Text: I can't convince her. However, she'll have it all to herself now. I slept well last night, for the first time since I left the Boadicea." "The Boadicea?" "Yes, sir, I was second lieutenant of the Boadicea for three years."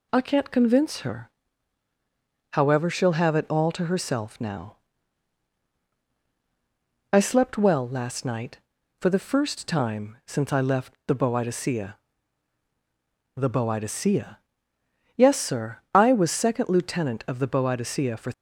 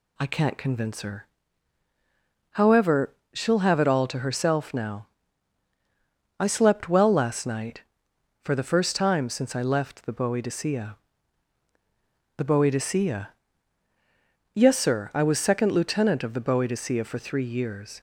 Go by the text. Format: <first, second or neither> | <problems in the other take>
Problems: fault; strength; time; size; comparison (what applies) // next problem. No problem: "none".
second | stops before "three years"; at 18.3 s